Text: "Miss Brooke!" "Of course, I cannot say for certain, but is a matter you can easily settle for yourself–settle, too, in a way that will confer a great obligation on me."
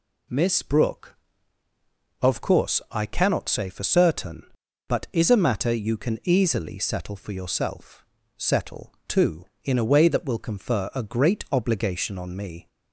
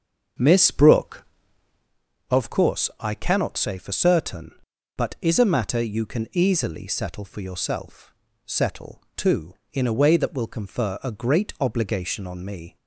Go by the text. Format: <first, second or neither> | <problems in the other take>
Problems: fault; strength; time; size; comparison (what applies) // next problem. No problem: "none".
first | starts louder than the rest; until 1.9 s; 7 dB